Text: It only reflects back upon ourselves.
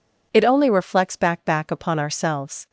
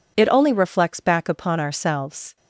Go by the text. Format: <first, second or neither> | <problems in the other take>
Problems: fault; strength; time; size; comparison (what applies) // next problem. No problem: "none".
second | says "back" twice; at 1.4 s